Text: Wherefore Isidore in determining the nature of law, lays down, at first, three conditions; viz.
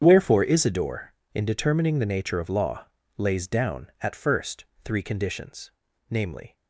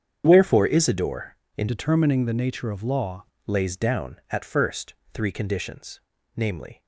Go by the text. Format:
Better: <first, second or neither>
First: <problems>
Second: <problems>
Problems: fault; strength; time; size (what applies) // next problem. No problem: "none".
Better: first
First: starts louder than the rest; strong; until 1.0 s; 7.5 dB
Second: starts louder than the rest; strong; until 1.2 s; 8 dB // changes voice from "determining" to "law"; from 1.6 to 3.2 s; 1.6 s long